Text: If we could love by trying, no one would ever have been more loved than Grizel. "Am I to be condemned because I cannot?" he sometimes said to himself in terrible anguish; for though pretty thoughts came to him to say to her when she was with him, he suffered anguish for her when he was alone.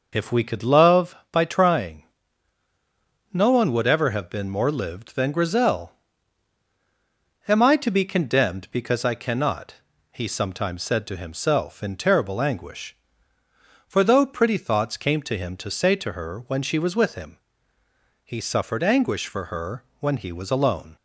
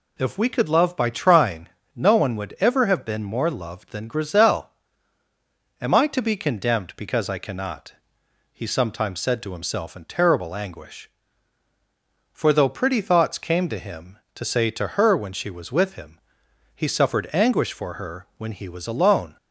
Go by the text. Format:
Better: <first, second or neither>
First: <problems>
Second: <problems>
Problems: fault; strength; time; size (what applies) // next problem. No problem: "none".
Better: second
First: says "lived" for "loved"; at 4.6 s // pauses between "her" and "when"; slight; at 19.8 s; 0.16 s long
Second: none